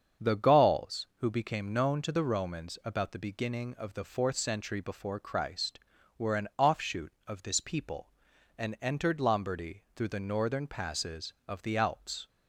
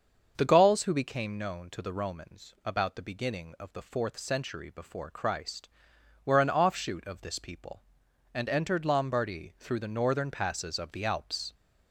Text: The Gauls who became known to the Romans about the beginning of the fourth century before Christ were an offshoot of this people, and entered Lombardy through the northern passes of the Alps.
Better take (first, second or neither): neither